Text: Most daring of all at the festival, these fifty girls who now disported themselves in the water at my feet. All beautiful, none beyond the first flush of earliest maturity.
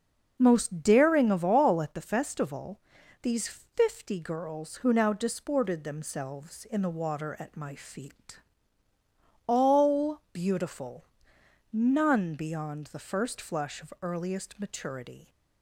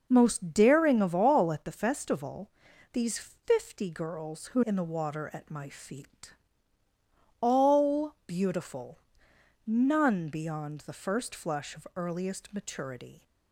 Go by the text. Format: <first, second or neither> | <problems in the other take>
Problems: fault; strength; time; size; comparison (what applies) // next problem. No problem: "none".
first | skips "now disported themselves"; at 4.6 s